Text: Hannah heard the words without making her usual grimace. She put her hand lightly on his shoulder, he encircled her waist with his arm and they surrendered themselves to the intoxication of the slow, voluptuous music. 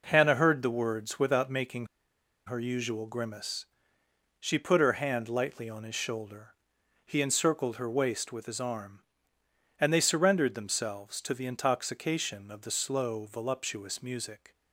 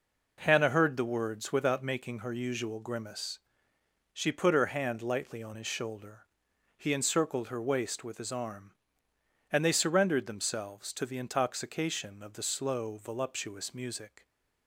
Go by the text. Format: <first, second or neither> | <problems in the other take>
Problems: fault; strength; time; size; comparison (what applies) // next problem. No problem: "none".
second | pauses between "making" and "her"; noticeable; at 1.8 s; 0.59 s long